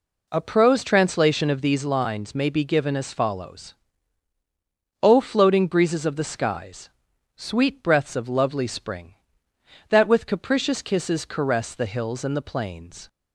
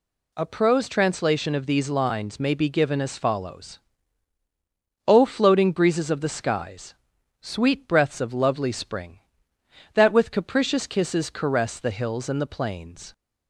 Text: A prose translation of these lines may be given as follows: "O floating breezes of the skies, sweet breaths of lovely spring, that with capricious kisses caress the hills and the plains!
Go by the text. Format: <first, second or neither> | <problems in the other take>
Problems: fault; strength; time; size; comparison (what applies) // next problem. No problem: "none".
second | starts louder than the rest; until 1.8 s; 3.5 dB